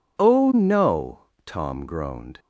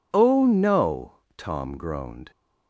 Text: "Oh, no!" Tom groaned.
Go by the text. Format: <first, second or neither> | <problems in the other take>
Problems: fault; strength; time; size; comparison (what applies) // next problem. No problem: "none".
neither | none